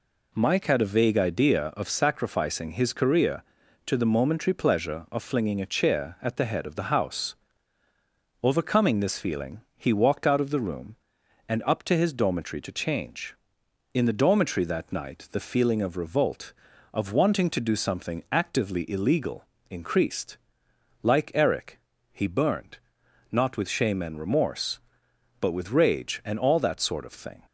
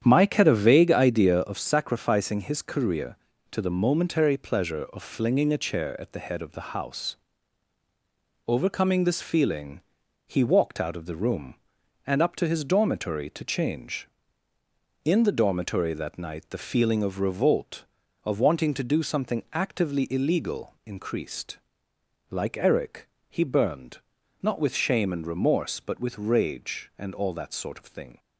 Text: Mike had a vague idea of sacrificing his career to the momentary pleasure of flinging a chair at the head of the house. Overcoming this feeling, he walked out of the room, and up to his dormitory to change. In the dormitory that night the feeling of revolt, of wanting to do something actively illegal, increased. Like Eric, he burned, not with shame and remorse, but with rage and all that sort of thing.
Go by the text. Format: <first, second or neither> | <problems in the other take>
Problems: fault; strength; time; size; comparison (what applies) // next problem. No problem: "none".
first | starts louder than the rest; strong; until 1.6 s; 9 dB